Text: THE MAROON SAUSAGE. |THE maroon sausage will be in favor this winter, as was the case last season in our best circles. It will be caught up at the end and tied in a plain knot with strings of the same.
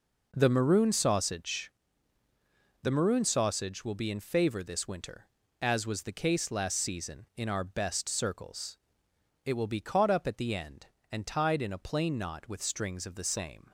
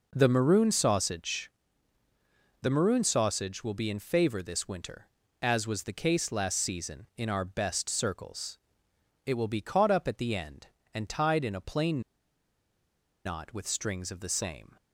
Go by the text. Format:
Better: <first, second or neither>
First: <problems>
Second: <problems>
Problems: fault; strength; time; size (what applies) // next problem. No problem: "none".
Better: first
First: none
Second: pauses between "plain" and "knot"; strong; at 11.9 s; 1.2 s long